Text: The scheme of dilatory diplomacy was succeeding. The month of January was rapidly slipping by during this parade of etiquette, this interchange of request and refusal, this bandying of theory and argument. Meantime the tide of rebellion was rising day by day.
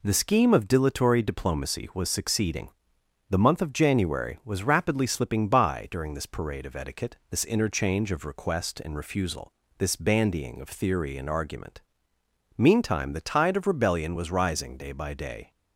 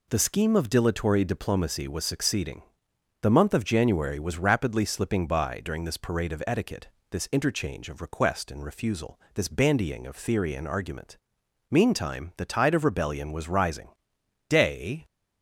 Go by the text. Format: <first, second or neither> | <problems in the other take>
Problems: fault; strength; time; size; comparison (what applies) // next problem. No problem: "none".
first | pauses between "rising" and "day"; noticeable; at 13.8 s; 0.60 s long // stops before "by day"; at 15.0 s